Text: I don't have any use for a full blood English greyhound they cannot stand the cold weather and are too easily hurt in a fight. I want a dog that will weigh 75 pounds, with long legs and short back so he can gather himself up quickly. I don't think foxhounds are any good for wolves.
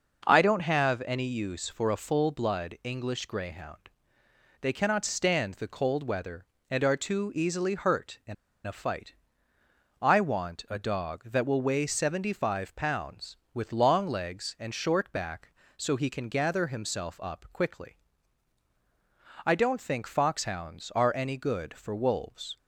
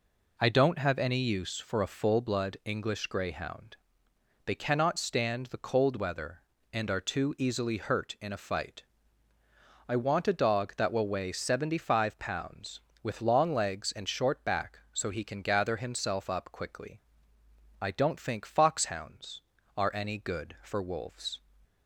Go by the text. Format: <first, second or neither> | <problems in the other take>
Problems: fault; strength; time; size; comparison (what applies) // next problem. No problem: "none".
second | pauses between "greyhound" and "they"; noticeable; at 3.8 s; 0.72 s long; noticeable in the second // pauses between "in" and "a"; slight; at 8.3 s; 0.32 s long